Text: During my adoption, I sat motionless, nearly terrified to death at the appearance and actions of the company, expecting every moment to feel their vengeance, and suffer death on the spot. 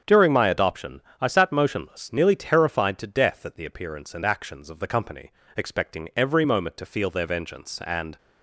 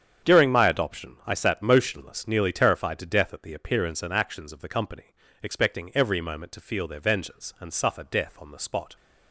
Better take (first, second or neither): second